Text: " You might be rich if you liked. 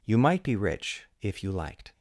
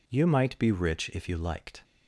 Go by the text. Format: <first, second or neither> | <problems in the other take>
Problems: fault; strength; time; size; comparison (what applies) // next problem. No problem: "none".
neither | none